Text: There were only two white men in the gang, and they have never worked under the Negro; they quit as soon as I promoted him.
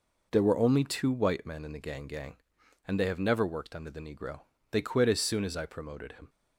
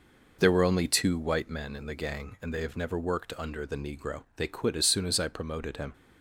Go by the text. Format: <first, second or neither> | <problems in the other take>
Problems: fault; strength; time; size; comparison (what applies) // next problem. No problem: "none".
second | says "gang" twice; at 2.0 s